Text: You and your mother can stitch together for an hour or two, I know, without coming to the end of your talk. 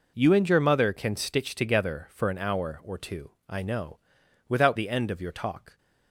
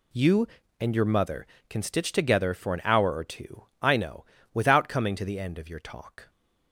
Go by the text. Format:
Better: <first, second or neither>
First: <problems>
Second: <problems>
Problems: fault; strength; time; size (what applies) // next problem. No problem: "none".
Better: second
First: skips "coming to"; at 4.7 s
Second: none